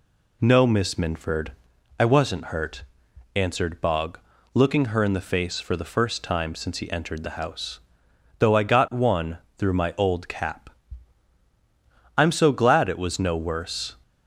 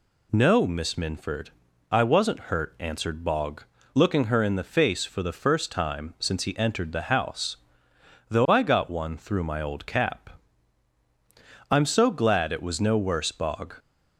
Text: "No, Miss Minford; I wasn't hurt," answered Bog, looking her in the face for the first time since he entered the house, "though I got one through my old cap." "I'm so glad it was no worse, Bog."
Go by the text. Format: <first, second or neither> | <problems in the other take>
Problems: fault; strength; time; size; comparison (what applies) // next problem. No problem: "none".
second | pauses between "one" and "through"; slight; at 9.3 s; 0.22 s long // stops before "Bog"; at 14.0 s